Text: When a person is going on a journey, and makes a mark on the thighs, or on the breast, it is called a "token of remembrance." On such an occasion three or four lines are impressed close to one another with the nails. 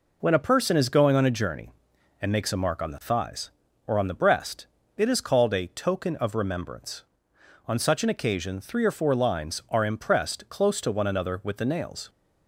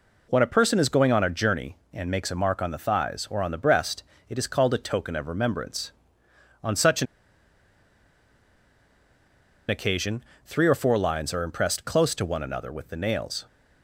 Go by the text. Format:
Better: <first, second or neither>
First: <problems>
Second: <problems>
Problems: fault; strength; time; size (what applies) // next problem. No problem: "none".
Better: first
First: none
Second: pauses between "an" and "occasion"; strong; at 7.0 s; 2.6 s long // pauses between "occasion" and "three"; slight; at 10.2 s; 0.22 s long